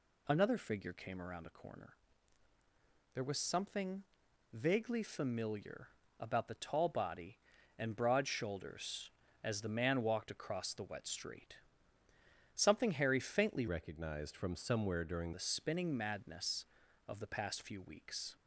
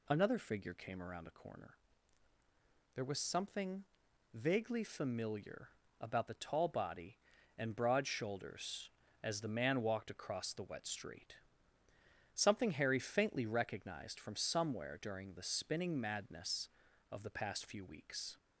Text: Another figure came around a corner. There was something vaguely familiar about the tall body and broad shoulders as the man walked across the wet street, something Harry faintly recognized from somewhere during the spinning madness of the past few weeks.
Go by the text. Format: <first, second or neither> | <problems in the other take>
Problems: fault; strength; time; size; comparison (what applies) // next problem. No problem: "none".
second | pauses between "something" and "vaguely"; noticeable; at 4.0 s; 0.48 s long; noticeable in the second // pauses between "familiar" and "about"; slight; at 5.8 s; 0.32 s long; slight in the second // changes voice from "recognized" to "during"; from 13.6 to 15.3 s; 1.7 s long